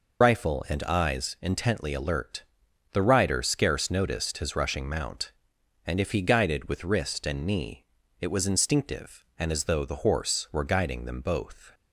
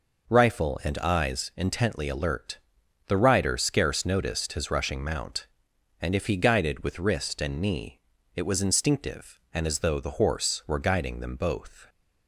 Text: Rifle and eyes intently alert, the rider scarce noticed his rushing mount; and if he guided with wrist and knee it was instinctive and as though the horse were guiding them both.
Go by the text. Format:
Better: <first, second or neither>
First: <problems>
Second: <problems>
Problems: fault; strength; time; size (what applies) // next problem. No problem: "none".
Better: second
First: loses the start of "Rifle"; at 0.2 s; 80 ms // pauses between "knee" and "it"; slight; at 7.8 s; 0.34 s long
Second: pauses between "knee" and "it"; slight; at 8.0 s; 0.34 s long